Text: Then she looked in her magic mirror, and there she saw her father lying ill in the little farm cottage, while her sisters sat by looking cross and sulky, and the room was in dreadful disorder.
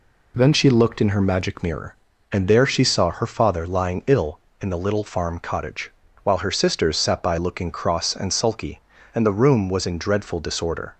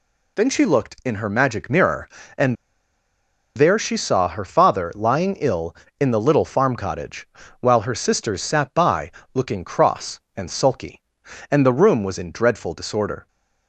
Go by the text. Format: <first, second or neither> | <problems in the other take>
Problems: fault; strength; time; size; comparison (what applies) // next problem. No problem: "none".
first | pauses between "and" and "there"; at 2.5 s; 1.0 s long // pauses between "by" and "looking"; slight; at 9.1 s; 0.22 s long